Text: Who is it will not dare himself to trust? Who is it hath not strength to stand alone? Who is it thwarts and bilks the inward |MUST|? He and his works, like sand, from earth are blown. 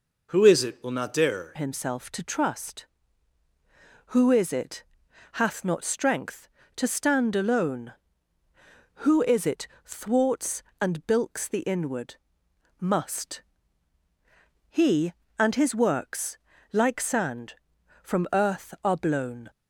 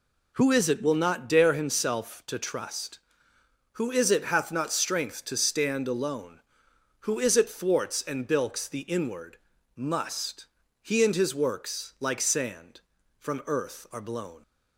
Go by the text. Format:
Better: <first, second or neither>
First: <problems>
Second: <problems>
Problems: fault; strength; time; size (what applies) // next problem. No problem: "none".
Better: second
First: changes voice at "himself"; from 1.5 s on; 17.9 s long // pauses between "it" and "hath"; noticeable; at 4.8 s; 0.50 s long // pauses between "it" and "thwarts"; slight; at 9.6 s; 0.18 s long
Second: none